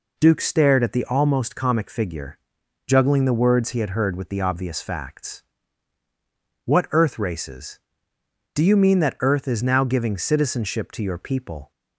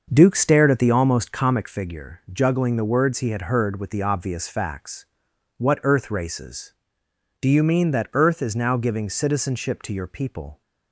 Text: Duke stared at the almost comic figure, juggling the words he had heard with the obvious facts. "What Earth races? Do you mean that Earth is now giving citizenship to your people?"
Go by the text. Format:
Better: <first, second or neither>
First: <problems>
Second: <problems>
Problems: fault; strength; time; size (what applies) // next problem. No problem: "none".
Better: first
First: none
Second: starts louder than the rest; until 1.8 s; 6 dB